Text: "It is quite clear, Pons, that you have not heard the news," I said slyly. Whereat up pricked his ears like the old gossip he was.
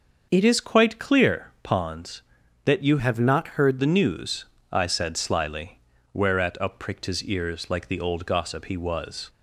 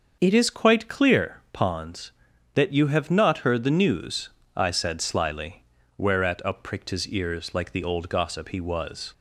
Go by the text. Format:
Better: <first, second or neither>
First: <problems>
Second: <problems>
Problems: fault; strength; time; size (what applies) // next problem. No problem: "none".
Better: second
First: starts louder than the rest; until 1.3 s; 6.5 dB // changes voice from "have" to "heard"; from 2.9 to 3.8 s; 0.9 s long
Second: starts louder than the rest; until 1.2 s; 6.5 dB